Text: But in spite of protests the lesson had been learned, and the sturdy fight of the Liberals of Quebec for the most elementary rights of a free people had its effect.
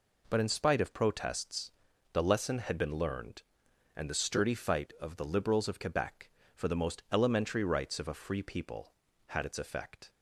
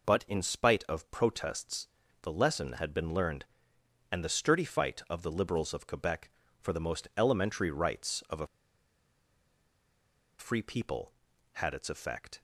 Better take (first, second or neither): first